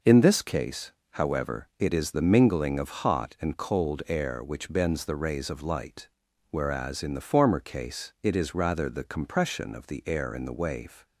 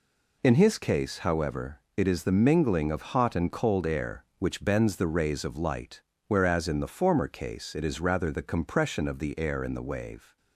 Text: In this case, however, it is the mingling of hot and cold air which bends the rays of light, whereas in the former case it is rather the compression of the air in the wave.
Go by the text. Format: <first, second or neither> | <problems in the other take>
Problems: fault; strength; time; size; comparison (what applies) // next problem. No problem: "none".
first | says "his" for "this"; at 0.5 s